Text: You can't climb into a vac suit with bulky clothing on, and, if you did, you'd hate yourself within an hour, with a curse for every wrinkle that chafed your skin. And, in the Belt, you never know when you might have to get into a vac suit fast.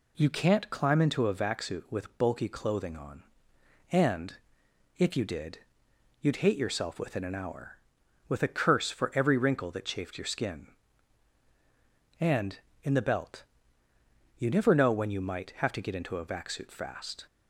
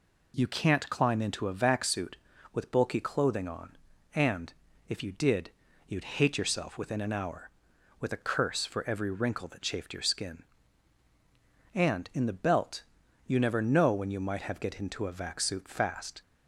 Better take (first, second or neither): first